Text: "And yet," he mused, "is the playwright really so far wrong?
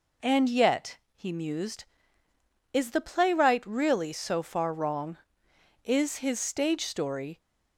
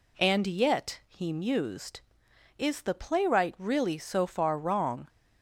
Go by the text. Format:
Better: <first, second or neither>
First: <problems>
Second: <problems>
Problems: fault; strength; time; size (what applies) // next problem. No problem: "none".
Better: second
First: goes on to say "Is his stage story"; from 5.8 s on; 1.5 s long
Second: none